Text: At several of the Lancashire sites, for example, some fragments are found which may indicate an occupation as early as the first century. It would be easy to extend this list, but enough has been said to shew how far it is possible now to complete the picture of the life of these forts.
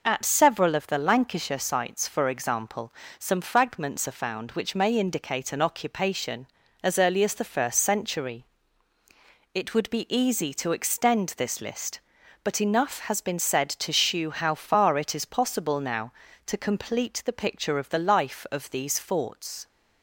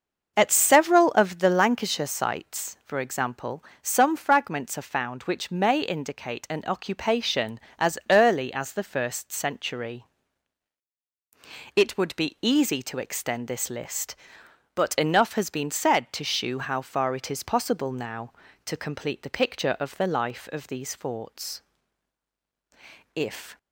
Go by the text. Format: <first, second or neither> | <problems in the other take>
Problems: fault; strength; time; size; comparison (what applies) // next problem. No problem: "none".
first | starts louder than the rest; until 1.3 s; 6 dB // goes on to say "If"; slight; from 23.1 s on; 0.44 s long